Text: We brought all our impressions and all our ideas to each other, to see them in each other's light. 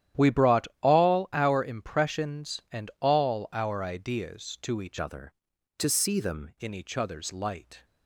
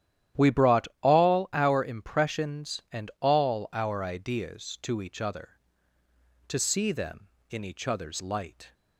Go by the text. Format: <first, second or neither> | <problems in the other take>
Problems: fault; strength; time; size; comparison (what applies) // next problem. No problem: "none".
second | starts louder than the rest; strong; until 1.3 s; 11 dB; strong in the second // changes voice from "other" to "them"; from 4.9 to 6.5 s; 1.6 s long